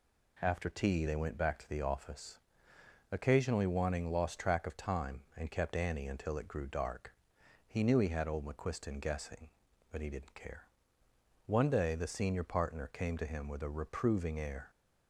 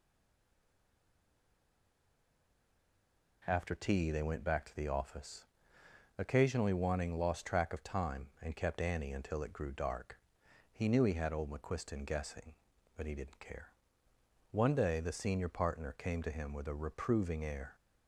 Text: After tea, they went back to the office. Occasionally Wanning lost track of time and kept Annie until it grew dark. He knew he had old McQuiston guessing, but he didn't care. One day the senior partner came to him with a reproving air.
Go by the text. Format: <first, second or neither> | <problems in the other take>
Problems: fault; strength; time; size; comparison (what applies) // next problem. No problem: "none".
first | stays silent before the first word; strong; until 3.4 s; 3.4 s long